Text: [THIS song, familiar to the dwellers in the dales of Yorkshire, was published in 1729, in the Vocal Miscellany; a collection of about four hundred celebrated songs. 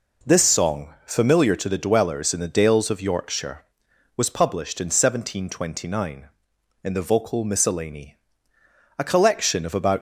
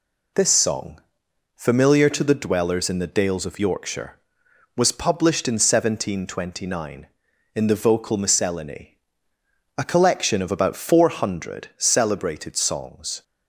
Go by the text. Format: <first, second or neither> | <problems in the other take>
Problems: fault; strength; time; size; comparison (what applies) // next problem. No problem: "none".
second | stops before "four hundred celebrated songs"; at 9.9 s